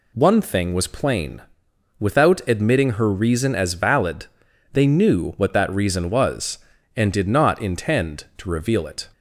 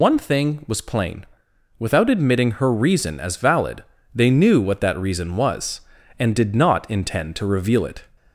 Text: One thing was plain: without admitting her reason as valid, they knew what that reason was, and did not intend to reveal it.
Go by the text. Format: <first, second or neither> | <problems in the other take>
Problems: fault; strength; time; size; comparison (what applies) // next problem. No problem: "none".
first | loses the start of "One"; at 0.0 s; 80 ms